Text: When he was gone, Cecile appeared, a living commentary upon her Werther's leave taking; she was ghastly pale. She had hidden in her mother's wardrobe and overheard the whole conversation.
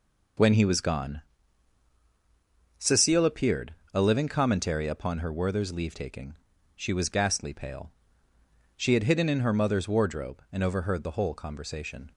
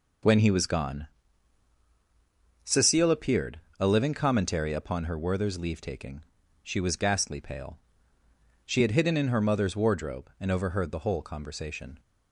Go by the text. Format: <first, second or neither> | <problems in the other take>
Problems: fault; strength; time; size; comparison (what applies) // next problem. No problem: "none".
neither | none